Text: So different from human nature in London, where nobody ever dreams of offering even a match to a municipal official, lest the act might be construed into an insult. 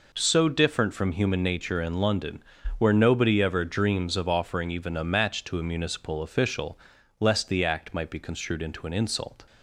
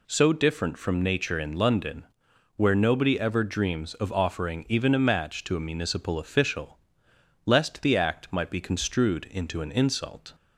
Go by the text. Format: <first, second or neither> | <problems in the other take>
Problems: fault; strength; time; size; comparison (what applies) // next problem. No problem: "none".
first | skips "human"; at 1.0 s